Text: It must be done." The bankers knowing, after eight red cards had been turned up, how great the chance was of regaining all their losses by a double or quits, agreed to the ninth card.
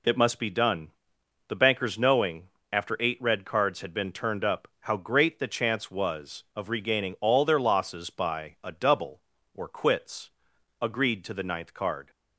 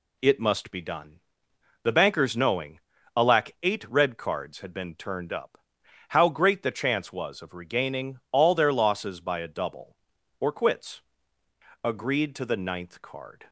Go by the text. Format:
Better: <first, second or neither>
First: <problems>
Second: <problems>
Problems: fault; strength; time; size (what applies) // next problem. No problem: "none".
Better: first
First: none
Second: says "alack" for "after"; at 3.1 s